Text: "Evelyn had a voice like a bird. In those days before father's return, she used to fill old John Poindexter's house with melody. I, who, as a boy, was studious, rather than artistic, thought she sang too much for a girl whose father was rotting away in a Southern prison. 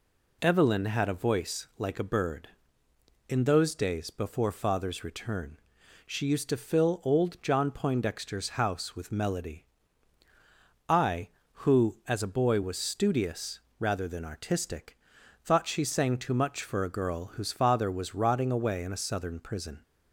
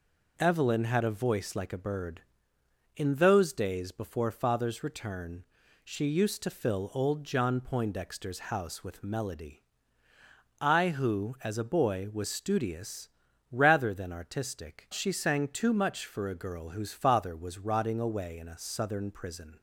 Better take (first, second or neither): first